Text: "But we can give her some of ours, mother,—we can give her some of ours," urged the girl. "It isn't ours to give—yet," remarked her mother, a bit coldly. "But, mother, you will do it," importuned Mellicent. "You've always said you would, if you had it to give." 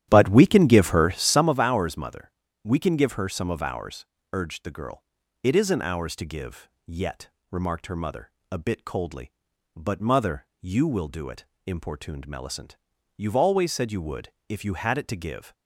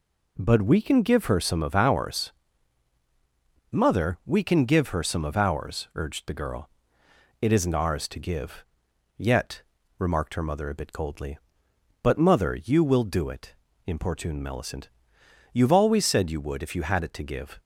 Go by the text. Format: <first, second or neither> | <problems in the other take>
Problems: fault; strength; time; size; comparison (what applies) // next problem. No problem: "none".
second | starts louder than the rest; strong; until 1.5 s; 11.5 dB